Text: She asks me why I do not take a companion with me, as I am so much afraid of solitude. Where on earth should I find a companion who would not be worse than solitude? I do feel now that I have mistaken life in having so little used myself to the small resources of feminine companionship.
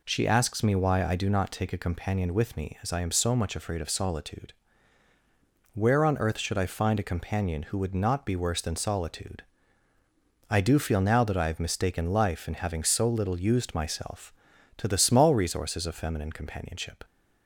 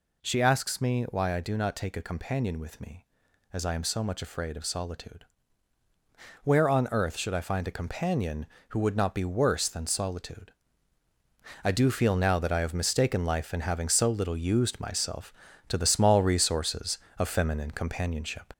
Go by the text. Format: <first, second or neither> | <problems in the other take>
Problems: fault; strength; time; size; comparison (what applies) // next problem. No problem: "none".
first | gets louder; throughout; 4 dB